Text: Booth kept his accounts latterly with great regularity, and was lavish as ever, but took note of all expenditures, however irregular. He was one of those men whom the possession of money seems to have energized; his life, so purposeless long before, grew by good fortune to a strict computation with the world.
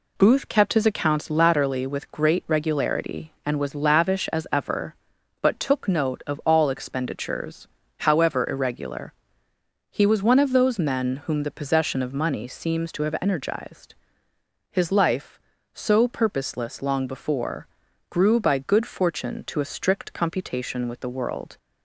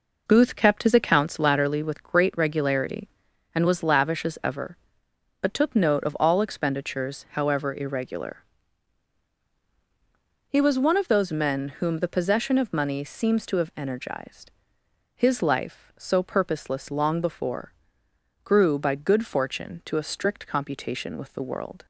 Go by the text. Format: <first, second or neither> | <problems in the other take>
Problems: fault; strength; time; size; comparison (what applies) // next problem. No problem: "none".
first | starts louder than the rest; noticeable; until 1.4 s; 4.5 dB